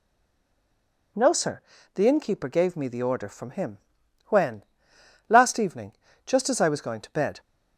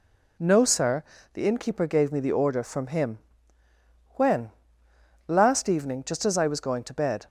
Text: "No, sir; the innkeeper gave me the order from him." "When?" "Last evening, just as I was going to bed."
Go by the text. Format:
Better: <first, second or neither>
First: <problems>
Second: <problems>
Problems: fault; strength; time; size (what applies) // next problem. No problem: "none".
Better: second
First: stays silent before the first word; until 1.1 s; 1.1 s long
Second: none